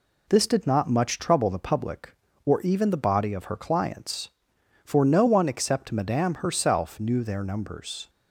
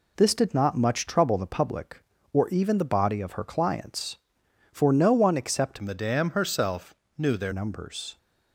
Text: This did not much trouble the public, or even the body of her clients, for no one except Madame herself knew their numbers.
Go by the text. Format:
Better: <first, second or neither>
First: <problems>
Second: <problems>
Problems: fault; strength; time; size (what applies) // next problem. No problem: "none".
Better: first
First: none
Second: changes voice from "Madame" to "their"; from 5.8 to 7.5 s; 1.7 s long // pauses between "herself" and "knew"; slight; at 6.9 s; 0.24 s long